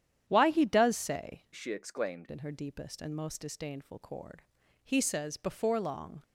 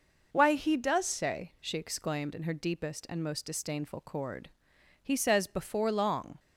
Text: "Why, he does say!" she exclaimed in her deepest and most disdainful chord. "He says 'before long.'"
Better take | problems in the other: second | starts louder than the rest; strong; until 1.2 s; 9.5 dB // changes voice from "she" to "exclaimed"; from 1.5 to 2.2 s; 0.7 s long

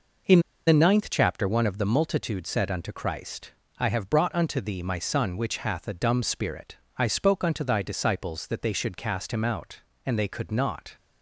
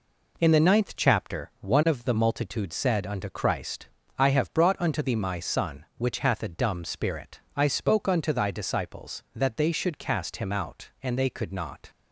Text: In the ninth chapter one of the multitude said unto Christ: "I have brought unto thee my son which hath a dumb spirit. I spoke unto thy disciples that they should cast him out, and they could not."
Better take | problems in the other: second | pauses between "In" and "the"; slight; at 0.4 s; 0.26 s long

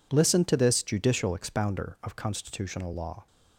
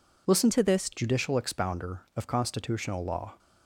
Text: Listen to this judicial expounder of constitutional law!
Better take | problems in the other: first | changes voice from "to" to "this"; from 0.5 to 0.9 s; 0.4 s long

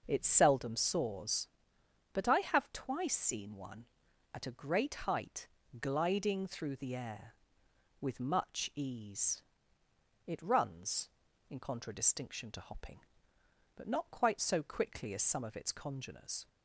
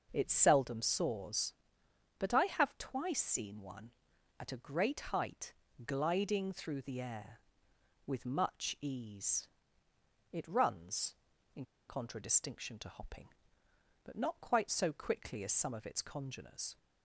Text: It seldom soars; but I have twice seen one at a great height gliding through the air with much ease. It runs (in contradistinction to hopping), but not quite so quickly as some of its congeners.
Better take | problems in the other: first | pauses between "great" and "height"; slight; at 4.9 s; 0.16 s long; slight in the first // pauses between "height" and "gliding"; slight; at 5.5 s; 0.32 s long; slight in the first // pauses between "in" and "contradistinction"; slight; at 11.6 s; 0.23 s long

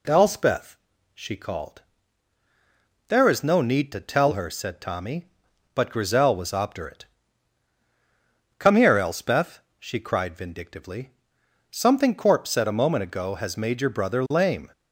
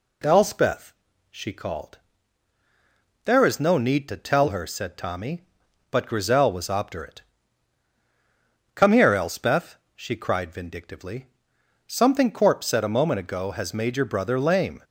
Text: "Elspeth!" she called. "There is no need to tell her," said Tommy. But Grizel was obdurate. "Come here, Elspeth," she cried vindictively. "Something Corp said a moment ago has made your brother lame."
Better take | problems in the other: neither | none

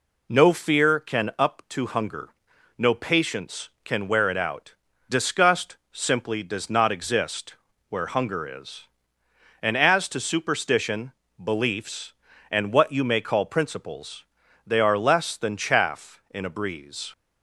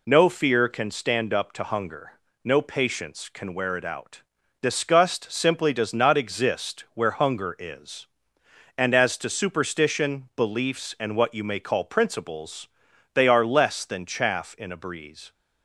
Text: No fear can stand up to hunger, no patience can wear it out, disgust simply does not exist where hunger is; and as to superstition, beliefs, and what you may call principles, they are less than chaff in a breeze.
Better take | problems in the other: second | skips "stand"; at 1.3 s // pauses between "disgust" and "simply"; slight; at 5.7 s; 0.16 s long // pauses between "exist" and "where"; slight; at 7.5 s; 0.34 s long

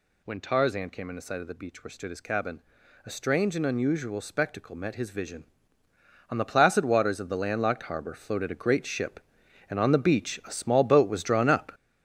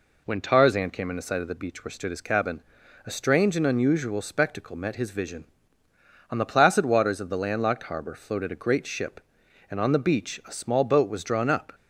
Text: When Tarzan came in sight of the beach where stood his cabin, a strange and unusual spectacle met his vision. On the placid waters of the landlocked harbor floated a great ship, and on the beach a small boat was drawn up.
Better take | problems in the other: second | gets louder; strong; throughout; 8.5 dB

